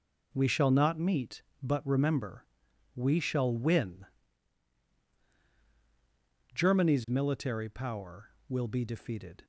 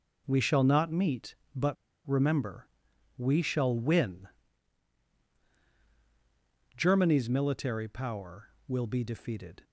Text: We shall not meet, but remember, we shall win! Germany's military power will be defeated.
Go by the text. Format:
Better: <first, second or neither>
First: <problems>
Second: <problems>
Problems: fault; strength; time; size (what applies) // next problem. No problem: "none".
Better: first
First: none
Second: pauses between "but" and "remember"; slight; at 1.7 s; 0.32 s long